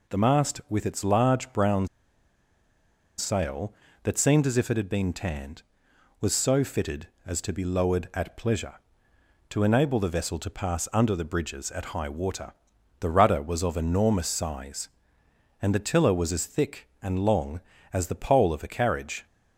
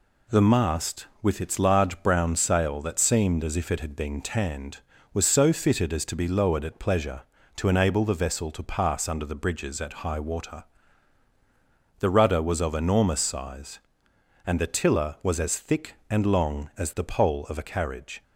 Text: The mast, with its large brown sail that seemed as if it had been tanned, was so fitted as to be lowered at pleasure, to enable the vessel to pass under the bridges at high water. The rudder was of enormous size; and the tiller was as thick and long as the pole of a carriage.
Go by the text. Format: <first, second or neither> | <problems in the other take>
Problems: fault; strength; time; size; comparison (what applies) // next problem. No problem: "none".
second | pauses between "brown" and "sail"; strong; at 1.8 s; 1.3 s long